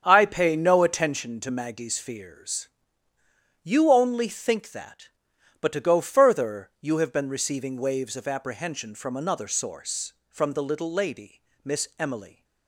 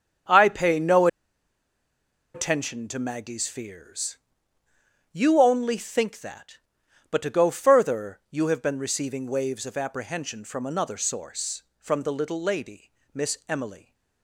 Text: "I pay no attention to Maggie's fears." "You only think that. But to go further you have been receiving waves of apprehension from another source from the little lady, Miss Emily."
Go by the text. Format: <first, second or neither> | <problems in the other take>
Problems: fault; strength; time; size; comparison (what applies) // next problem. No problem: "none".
first | starts louder than the rest; strong; until 2.5 s; 8 dB; strong in the first // pauses between "no" and "attention"; strong; at 1.0 s; 1.2 s long